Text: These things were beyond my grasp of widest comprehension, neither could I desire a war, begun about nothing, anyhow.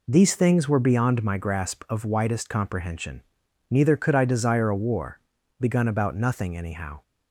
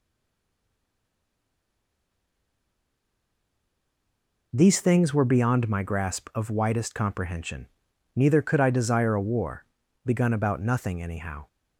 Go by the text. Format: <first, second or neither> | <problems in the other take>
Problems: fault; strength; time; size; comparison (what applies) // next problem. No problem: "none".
first | stays silent before the first word; strong; until 4.5 s; 4.5 s long